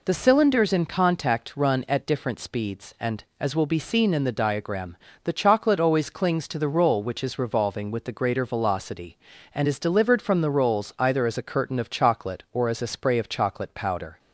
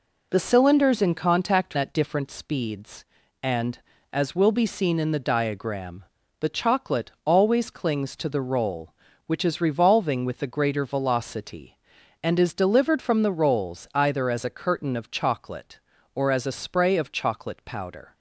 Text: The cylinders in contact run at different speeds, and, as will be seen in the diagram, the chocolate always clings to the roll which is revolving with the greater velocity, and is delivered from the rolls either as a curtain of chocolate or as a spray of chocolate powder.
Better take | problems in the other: first | skips "run"; at 1.7 s // pauses between "chocolate" and "always"; slight; at 7.0 s; 0.16 s long

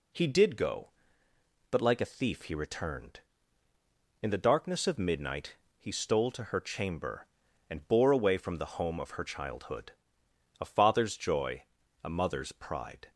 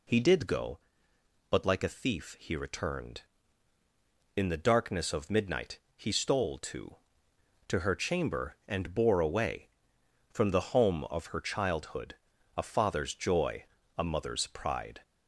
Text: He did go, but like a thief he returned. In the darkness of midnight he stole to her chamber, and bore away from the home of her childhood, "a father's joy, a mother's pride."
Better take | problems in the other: first | pauses between "midnight" and "he"; slight; at 5.8 s; 0.18 s long; slight in the first // says "to" twice; at 7.6 s

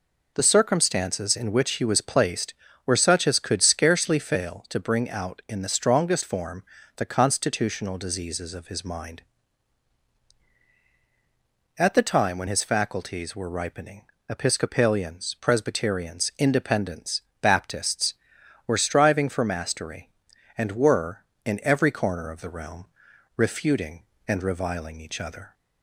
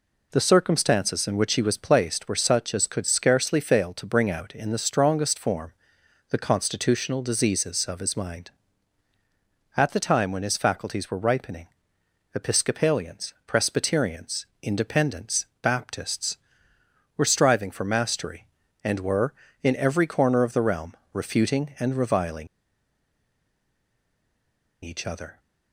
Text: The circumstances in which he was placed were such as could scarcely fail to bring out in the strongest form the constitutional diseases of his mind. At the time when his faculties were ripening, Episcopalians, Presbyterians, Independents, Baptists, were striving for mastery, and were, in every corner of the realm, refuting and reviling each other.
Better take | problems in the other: first | pauses between "form" and "the"; noticeable; at 5.7 s; 0.58 s long; slight in the first // pauses between "reviling" and "each"; strong; at 22.4 s; 2.3 s long

